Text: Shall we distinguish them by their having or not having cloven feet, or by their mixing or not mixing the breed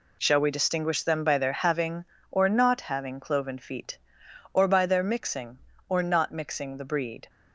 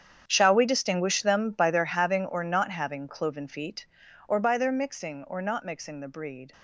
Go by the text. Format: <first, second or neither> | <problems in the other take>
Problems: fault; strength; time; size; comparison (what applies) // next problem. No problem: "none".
first | gets quieter; strong; throughout; 16 dB